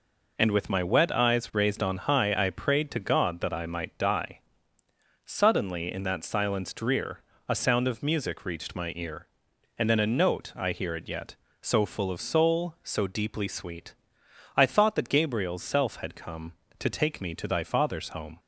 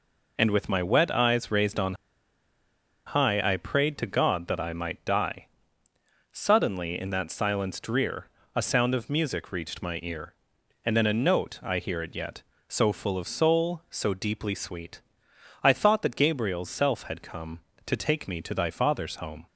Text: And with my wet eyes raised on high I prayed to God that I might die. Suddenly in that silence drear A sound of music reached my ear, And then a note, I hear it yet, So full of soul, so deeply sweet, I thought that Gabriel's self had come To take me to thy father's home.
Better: first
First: pauses between "drear" and "A"; slight; at 7.2 s; 0.28 s long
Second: pauses between "on" and "high"; at 1.9 s; 1.1 s long // pauses between "drear" and "A"; slight; at 8.2 s; 0.28 s long

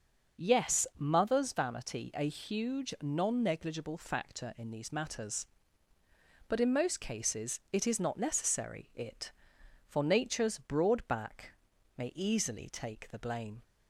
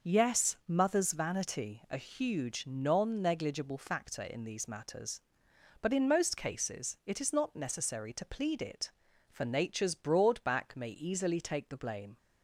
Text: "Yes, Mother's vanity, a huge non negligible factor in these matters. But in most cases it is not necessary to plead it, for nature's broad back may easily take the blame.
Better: second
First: starts louder than the rest; noticeable; until 1.4 s; 6 dB // skips "to plead"; at 8.9 s // pauses between "back" and "may"; at 11.5 s; 0.44 s long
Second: none

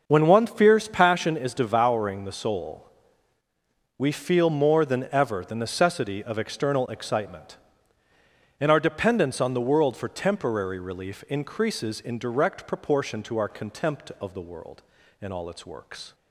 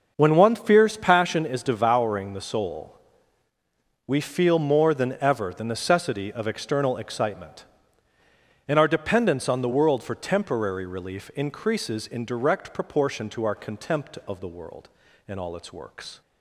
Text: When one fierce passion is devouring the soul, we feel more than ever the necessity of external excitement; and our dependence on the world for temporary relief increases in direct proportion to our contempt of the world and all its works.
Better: neither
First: starts louder than the rest; until 1.0 s; 6 dB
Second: starts louder than the rest; until 1.1 s; 6 dB

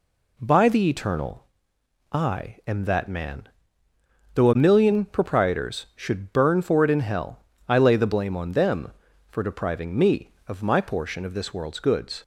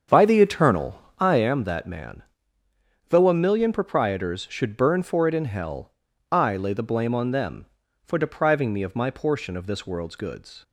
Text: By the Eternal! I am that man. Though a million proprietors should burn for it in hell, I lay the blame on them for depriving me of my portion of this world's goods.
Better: first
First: none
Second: starts louder than the rest; strong; until 1.5 s; 7.5 dB

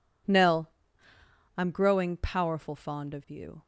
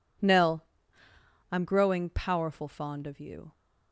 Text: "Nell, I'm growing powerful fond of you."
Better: neither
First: none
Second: none

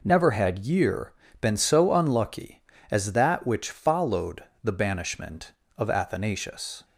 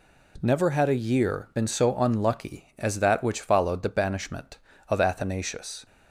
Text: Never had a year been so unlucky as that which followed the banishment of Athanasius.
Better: second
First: skips "a"; at 0.6 s // pauses between "year" and "been"; slight; at 1.1 s; 0.28 s long // pauses between "followed" and "the"; slight; at 4.4 s; 0.20 s long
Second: none

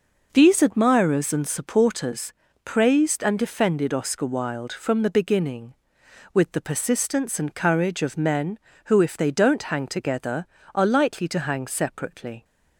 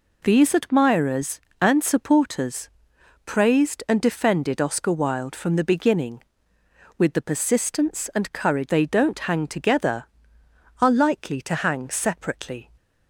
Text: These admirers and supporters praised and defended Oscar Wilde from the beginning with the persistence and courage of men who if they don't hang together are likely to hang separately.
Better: first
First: pauses between "supporters" and "praised"; slight; at 2.3 s; 0.32 s long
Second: pauses between "supporters" and "praised"; noticeable; at 2.6 s; 0.58 s long // skips "of men who if"; at 8.6 s

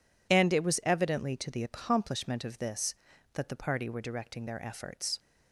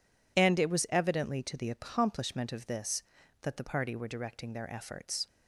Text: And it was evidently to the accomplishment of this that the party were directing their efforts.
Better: neither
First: none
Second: none

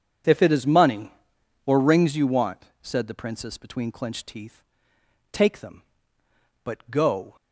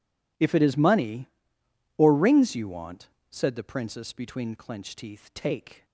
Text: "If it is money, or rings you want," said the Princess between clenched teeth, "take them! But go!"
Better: first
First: none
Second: stops before "them But go"; at 5.8 s

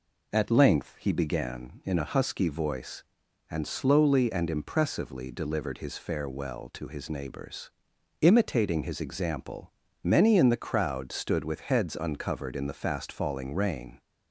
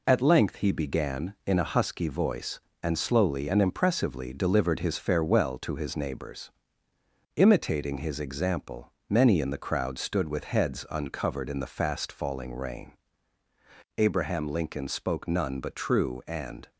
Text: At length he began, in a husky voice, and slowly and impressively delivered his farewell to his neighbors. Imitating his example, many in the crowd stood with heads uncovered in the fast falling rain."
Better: first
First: none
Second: goes on to say "Abraham Lincoln spoke none but true and"; strong; from 13.9 s on; 2.7 s long

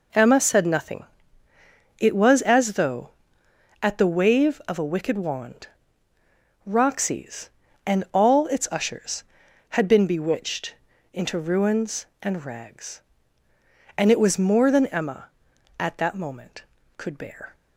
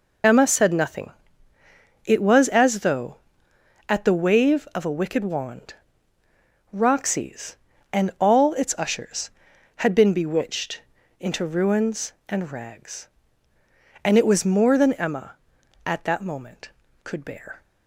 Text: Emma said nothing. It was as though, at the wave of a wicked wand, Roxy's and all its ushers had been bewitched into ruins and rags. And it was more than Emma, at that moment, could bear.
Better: first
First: pauses between "bewitched" and "into"; at 10.7 s; 0.38 s long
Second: loses the start of "Emma"; at 0.2 s; 55 ms // pauses between "bewitched" and "into"; at 10.8 s; 0.38 s long

